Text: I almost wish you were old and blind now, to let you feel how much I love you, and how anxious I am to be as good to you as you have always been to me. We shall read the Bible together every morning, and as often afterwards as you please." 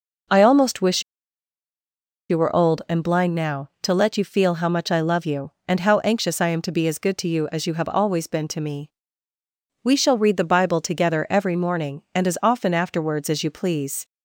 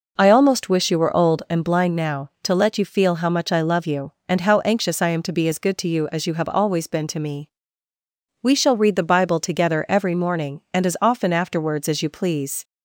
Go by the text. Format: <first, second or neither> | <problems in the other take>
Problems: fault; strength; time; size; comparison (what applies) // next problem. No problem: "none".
second | pauses between "wish" and "you"; strong; at 1.0 s; 1.2 s long